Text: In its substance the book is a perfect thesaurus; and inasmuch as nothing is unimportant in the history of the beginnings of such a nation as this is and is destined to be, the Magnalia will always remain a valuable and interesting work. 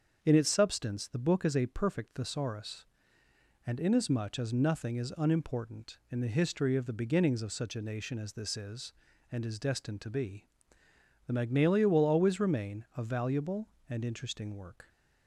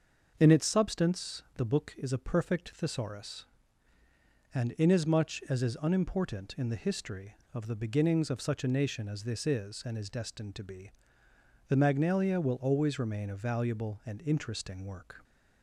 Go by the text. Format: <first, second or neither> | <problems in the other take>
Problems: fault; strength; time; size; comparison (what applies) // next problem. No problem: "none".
first | starts louder than the rest; until 1.4 s; 6 dB; also in the first // skips "nothing"; at 5.6 s